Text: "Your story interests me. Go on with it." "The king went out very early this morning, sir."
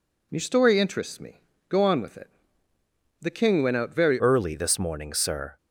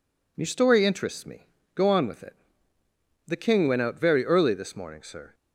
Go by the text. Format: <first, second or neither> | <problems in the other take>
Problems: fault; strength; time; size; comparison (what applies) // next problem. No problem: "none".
second | changes voice at "early"; from 4.1 s on; 1.4 s long